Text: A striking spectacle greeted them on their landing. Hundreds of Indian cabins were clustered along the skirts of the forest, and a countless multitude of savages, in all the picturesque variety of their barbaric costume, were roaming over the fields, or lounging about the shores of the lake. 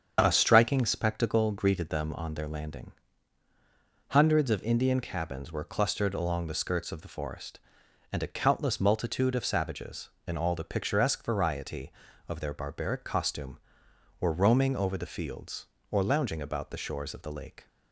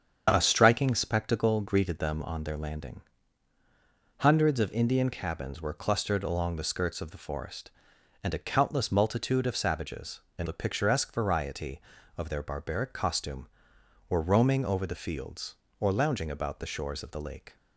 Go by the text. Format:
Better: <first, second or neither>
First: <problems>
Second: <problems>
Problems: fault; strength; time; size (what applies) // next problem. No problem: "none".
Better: first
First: starts louder than the rest; strong; until 1.2 s; 7.5 dB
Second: starts louder than the rest; strong; until 1.3 s; 7.5 dB // skips "all"; at 10.4 s